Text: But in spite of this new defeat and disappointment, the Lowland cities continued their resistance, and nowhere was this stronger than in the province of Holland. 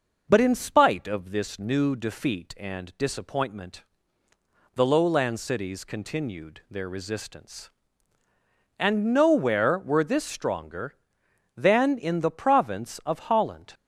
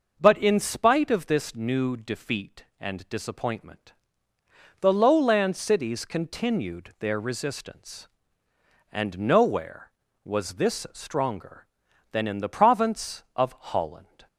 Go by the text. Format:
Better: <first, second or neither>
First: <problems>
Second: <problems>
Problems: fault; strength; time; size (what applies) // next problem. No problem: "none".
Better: second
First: says "were" for "was"; at 9.7 s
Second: none